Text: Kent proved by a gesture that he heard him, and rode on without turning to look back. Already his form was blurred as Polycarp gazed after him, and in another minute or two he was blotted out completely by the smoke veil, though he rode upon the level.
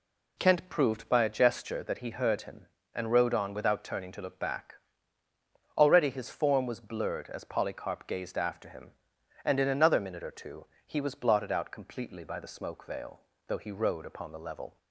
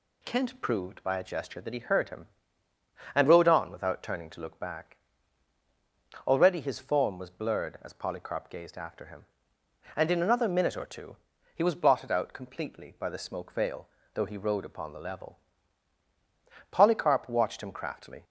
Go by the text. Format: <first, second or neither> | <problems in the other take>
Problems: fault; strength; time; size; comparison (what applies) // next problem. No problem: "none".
first | pauses between "two" and "he"; at 11.1 s; 0.40 s long; slight in the first // goes on to say "Polycarp watched him craftily"; from 16.6 s on; 1.5 s long